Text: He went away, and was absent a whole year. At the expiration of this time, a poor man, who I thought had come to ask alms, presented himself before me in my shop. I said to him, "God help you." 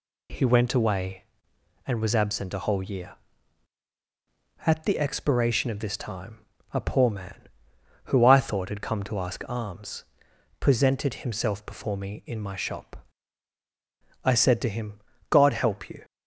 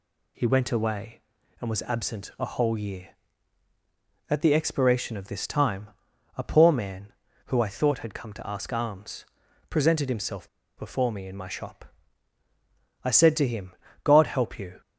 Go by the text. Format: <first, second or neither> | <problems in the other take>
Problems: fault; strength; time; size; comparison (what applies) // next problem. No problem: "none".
first | pauses between "himself" and "before"; slight; at 10.4 s; 0.30 s long